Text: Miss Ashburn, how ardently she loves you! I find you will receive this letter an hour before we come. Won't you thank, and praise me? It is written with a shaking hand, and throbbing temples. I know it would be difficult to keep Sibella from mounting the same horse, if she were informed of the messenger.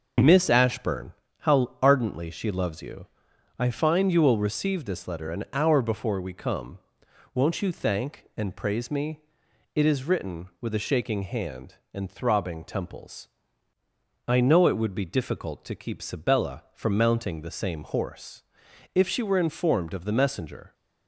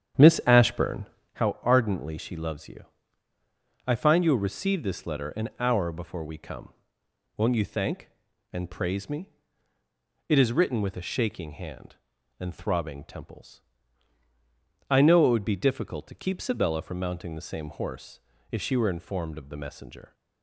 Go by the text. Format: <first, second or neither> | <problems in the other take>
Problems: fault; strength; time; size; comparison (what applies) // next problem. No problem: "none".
first | starts louder than the rest; strong; until 1.3 s; 9 dB